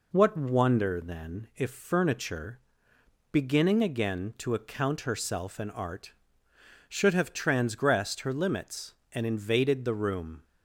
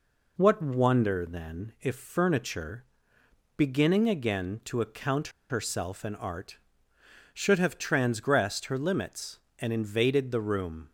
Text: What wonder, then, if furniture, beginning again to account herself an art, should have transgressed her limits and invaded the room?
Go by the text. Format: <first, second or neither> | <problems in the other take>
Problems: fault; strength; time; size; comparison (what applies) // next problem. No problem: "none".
first | pauses between "account" and "herself"; slight; at 5.2 s; 0.20 s long